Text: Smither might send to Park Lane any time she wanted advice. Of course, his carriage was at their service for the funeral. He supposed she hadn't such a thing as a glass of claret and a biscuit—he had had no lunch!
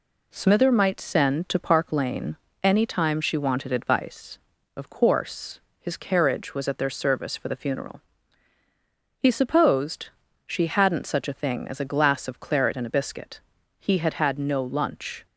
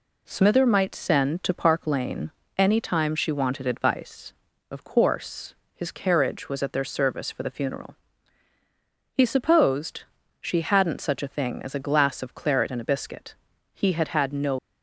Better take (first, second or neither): first